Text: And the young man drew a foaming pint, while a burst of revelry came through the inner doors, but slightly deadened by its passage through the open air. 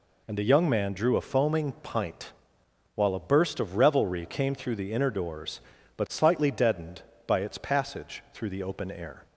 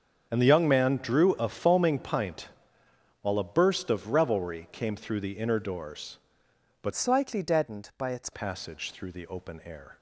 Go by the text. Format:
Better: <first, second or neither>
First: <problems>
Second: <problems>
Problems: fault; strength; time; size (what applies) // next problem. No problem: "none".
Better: first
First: none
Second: starts louder than the rest; strong; until 1.3 s; 7 dB // changes voice from "slightly" to "its"; from 6.9 to 8.2 s; 1.3 s long